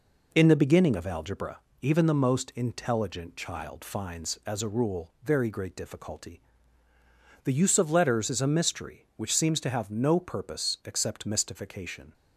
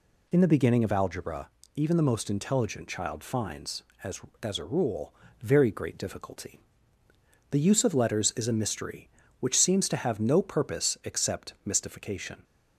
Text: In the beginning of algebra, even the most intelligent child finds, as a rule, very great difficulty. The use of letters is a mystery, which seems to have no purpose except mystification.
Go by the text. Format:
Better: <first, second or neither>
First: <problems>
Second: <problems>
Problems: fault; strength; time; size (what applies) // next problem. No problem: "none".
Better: first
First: none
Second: says "as" twice; at 4.4 s